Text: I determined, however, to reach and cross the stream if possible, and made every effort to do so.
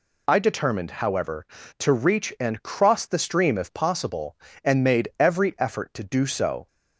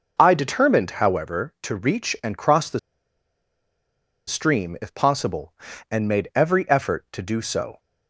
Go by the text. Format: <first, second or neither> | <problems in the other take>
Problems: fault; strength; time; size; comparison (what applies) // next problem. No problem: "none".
first | pauses between "the" and "stream"; strong; at 2.7 s; 1.4 s long